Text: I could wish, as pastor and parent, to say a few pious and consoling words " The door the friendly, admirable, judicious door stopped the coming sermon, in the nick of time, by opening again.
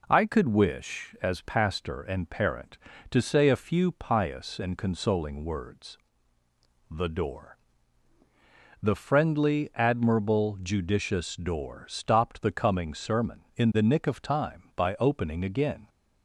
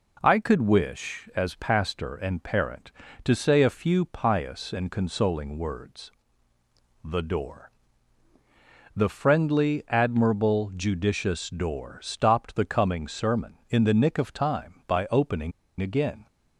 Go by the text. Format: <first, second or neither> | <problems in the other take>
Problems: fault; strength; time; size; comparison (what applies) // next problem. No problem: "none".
first | pauses between "door" and "the"; strong; at 7.6 s; 1.3 s long; strong in the first // pauses between "opening" and "again"; slight; at 15.5 s; 0.29 s long